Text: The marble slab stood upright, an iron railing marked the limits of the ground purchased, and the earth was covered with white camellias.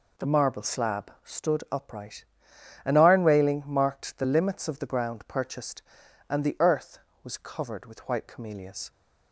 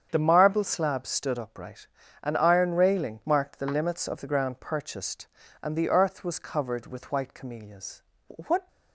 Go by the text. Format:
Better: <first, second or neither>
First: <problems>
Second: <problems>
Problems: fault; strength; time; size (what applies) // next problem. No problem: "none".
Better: first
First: none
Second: starts louder than the rest; strong; until 1.1 s; 8 dB // goes on to say "What"; slight; from 8.2 s on; 0.40 s long